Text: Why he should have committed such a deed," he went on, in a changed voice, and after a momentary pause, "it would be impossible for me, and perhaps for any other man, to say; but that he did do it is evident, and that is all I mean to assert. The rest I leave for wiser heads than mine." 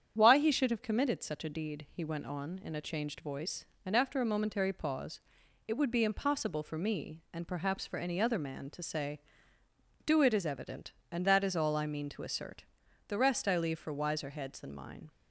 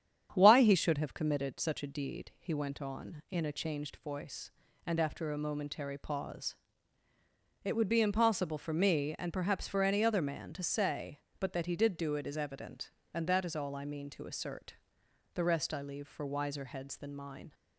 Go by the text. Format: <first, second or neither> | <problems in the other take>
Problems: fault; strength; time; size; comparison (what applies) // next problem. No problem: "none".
second | starts louder than the rest; strong; until 1.1 s; 8.5 dB; strong in the second // skips "but that he did"; at 9.6 s